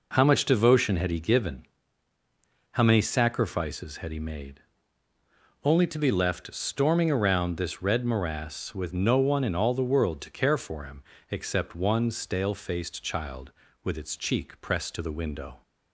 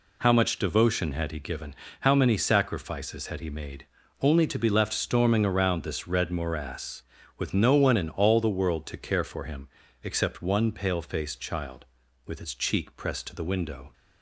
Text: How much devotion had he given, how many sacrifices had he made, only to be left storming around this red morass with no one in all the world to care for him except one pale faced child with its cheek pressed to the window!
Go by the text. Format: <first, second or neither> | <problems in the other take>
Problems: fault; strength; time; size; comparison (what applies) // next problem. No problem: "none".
second | pauses between "him" and "except"; slight; at 11.0 s; 0.28 s long; slight in the second // says "stale" for "pale"; at 12.0 s